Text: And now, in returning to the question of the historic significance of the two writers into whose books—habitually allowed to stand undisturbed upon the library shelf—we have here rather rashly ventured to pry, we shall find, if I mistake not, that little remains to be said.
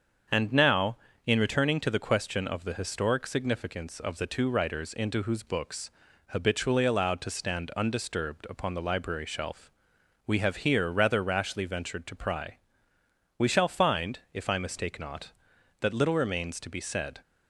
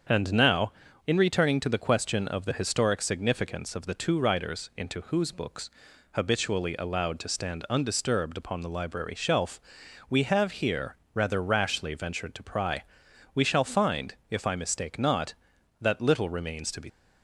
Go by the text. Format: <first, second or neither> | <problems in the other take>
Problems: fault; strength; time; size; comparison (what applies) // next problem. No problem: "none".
first | starts louder than the rest; strong; until 1.4 s; 7.5 dB; also in the first // pauses between "here" and "rather"; slight; at 10.9 s; 0.18 s long // stops before "said"; at 16.8 s